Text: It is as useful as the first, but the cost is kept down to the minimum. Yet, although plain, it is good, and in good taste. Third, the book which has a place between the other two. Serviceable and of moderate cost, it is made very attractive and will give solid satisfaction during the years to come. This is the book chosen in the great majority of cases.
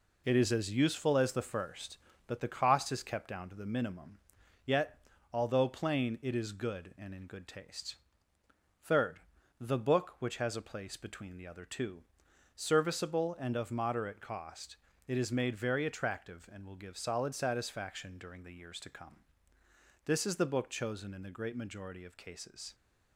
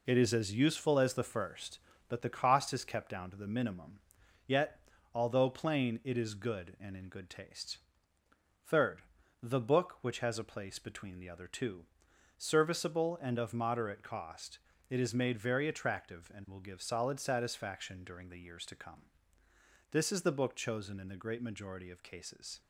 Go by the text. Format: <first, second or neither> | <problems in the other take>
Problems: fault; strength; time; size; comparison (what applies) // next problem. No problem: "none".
neither | none